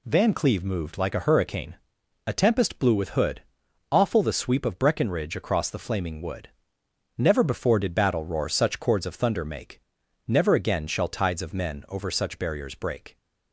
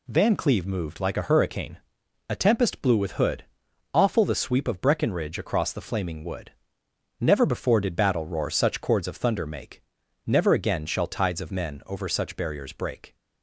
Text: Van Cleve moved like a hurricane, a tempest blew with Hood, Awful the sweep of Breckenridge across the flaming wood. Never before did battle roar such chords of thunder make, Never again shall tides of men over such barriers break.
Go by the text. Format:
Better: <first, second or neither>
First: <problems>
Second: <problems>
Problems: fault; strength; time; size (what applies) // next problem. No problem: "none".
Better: neither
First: none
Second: none